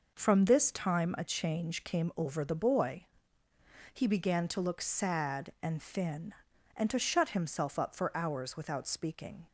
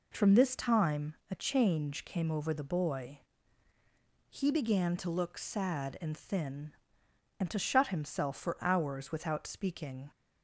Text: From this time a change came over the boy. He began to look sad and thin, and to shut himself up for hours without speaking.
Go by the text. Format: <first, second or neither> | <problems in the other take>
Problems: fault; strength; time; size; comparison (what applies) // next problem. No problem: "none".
first | pauses between "time" and "a"; slight; at 1.1 s; 0.16 s long // skips "up"; at 8.3 s